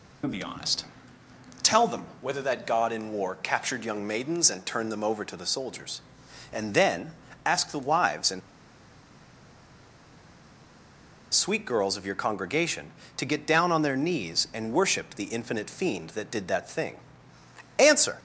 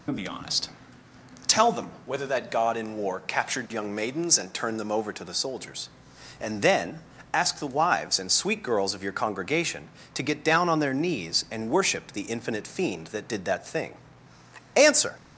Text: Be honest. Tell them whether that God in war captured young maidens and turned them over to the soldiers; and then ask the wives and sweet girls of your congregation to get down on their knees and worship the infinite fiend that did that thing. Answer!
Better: second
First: pauses between "them" and "whether"; slight; at 2.0 s; 0.16 s long // pauses between "then" and "ask"; slight; at 7.1 s; 0.34 s long // pauses between "and" and "sweet"; strong; at 8.4 s; 2.9 s long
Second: pauses between "them" and "whether"; slight; at 1.8 s; 0.16 s long // pauses between "then" and "ask"; slight; at 6.9 s; 0.34 s long

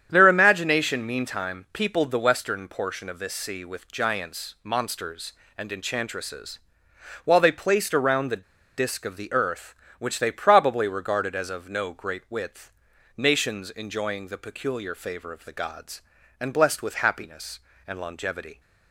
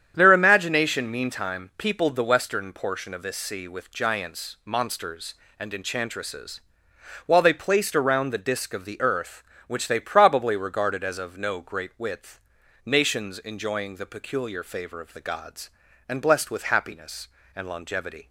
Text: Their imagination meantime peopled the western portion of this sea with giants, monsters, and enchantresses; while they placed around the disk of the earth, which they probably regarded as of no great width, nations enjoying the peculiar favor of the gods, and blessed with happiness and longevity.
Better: second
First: starts louder than the rest; strong; until 1.1 s; 9 dB // pauses between "the" and "disk"; slight; at 8.4 s; 0.34 s long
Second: starts louder than the rest; strong; until 1.1 s; 9 dB

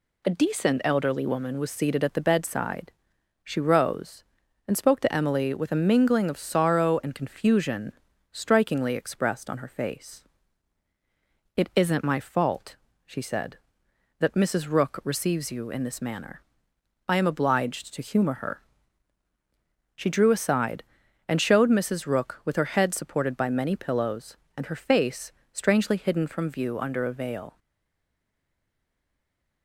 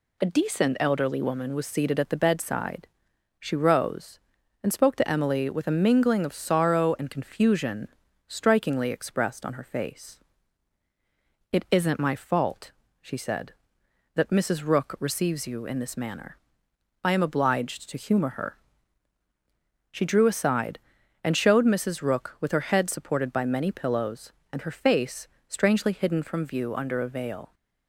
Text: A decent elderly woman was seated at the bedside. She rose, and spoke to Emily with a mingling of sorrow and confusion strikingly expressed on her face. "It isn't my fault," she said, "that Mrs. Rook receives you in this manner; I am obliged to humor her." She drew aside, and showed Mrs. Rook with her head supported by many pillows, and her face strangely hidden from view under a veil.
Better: second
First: pauses between "confusion" and "strikingly"; at 7.9 s; 0.40 s long // pauses between "face" and "strangely"; slight; at 25.3 s; 0.22 s long // stays silent after the last word; from 27.5 s on; 2.1 s long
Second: pauses between "confusion" and "strikingly"; at 7.8 s; 0.40 s long // pauses between "face" and "strangely"; slight; at 25.2 s; 0.22 s long

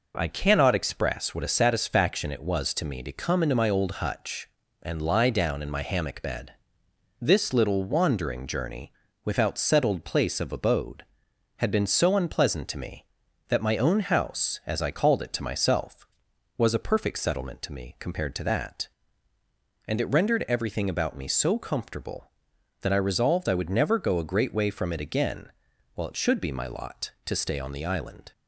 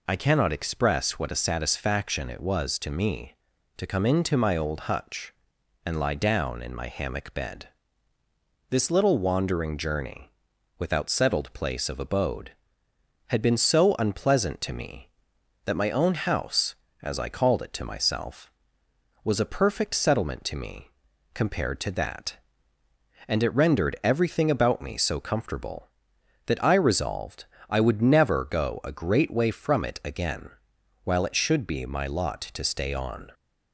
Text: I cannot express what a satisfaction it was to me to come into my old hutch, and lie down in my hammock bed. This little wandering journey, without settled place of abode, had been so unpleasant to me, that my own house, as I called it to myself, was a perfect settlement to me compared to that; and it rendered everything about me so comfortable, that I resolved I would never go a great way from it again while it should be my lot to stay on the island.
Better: first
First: pauses between "again" and "while"; at 25.5 s; 0.42 s long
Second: pauses between "me" and "compared"; noticeable; at 20.8 s; 0.46 s long // pauses between "resolved" and "I"; slight; at 27.4 s; 0.22 s long // pauses between "again" and "while"; noticeable; at 30.4 s; 0.54 s long // stops before "the island"; at 33.3 s

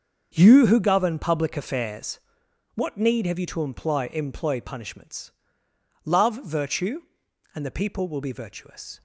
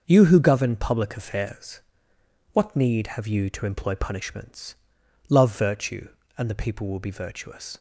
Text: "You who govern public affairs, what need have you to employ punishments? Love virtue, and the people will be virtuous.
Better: second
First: starts louder than the rest; until 1.3 s; 7 dB // says "employ" twice; at 4.1 s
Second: starts louder than the rest; until 1.0 s; 6 dB

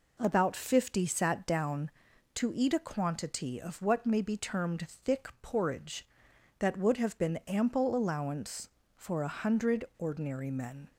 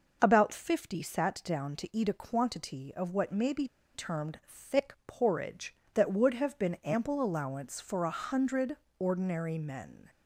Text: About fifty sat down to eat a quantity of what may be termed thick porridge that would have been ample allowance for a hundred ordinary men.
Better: first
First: none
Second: pauses between "be" and "termed"; slight; at 3.6 s; 0.26 s long // pauses between "hundred" and "ordinary"; slight; at 8.7 s; 0.24 s long

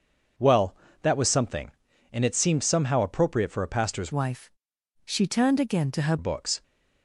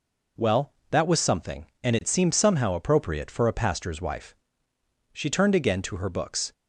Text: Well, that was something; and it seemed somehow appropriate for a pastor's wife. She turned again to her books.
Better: second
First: changes voice from "wife" to "her"; from 4.1 to 6.1 s; 2.0 s long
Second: none

